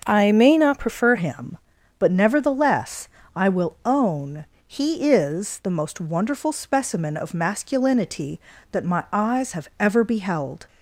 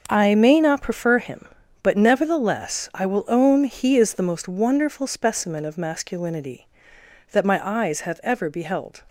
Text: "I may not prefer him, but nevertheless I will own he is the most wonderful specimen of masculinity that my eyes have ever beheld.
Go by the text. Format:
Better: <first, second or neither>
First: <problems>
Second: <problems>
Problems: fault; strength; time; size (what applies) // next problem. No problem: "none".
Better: second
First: starts louder than the rest; noticeable; until 1.0 s; 6 dB // changes voice at "him"; from 1.1 s on; 9.5 s long // pauses between "nevertheless" and "I"; slight; at 3.0 s; 0.28 s long // pauses between "own" and "he"; slight; at 4.4 s; 0.22 s long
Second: starts louder than the rest; noticeable; until 1.0 s; 6 dB